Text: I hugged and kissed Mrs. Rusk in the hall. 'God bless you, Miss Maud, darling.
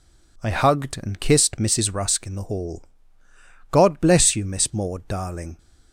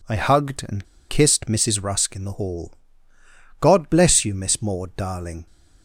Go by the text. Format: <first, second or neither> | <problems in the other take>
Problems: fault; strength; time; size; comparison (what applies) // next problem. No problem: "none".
first | pauses between "and" and "kissed"; slight; at 0.8 s; 0.24 s long